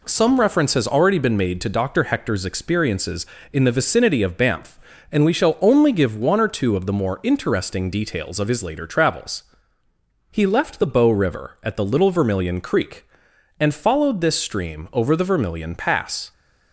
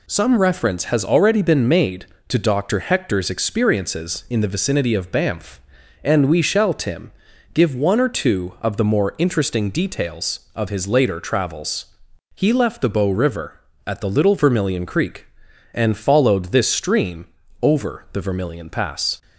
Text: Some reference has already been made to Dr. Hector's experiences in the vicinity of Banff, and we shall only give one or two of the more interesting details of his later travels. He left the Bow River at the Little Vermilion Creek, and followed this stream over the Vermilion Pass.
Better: first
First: none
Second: says "tim" for "only"; at 6.7 s // pauses between "stream" and "over"; slight; at 17.2 s; 0.34 s long

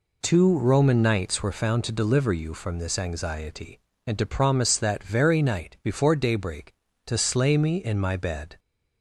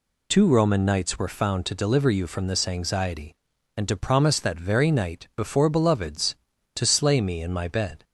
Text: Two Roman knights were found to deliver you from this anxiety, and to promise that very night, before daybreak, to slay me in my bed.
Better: first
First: none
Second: says "beloveds" for "daybreak"; at 5.6 s

